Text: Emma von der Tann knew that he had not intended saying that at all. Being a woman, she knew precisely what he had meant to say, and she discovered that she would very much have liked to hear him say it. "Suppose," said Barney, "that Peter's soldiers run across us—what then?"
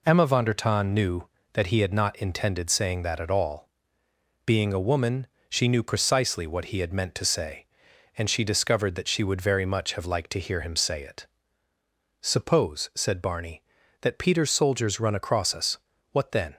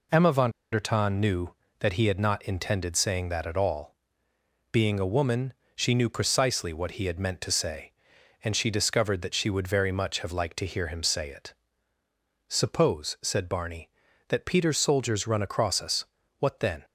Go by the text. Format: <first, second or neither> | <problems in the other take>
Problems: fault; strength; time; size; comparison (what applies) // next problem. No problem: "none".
first | pauses between "von" and "der"; slight; at 0.5 s; 0.22 s long